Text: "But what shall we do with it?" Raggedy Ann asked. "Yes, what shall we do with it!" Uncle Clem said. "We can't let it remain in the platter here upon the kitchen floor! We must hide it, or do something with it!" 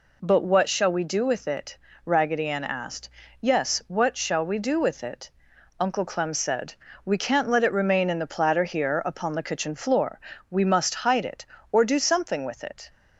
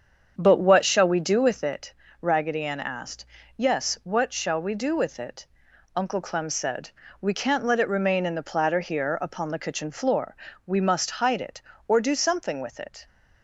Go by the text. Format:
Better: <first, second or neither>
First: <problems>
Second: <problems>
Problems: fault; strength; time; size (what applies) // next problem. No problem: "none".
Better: first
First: none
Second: starts louder than the rest; strong; until 1.8 s; 7.5 dB